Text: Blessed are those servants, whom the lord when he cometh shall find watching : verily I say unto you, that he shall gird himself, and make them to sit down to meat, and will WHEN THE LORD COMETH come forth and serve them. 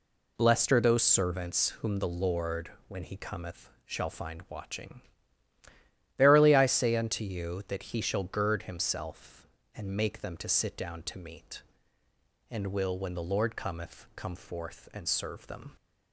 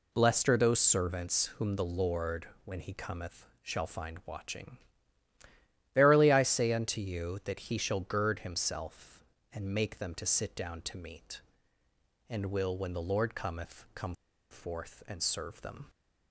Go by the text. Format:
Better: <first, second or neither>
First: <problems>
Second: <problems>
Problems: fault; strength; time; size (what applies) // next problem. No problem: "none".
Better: first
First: pauses between "lord" and "when"; slight; at 2.7 s; 0.18 s long // pauses between "cometh" and "shall"; slight; at 3.6 s; 0.16 s long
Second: pauses between "lord" and "when"; slight; at 2.4 s; 0.18 s long // pauses between "cometh" and "shall"; slight; at 3.4 s; 0.16 s long // pauses between "come" and "forth"; at 14.1 s; 0.38 s long